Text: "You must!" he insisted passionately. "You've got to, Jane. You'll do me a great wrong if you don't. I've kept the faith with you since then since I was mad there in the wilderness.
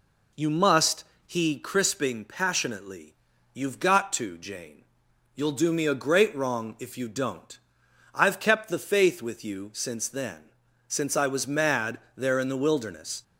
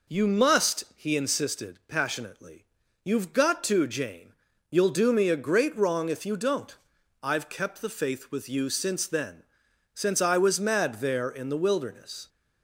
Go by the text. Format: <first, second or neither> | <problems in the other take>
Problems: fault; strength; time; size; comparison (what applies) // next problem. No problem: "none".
second | says "crisping" for "insisted"; at 1.5 s // pauses between "then" and "since"; at 10.4 s; 0.40 s long; noticeable in the second // pauses between "mad" and "there"; slight; at 11.9 s; 0.18 s long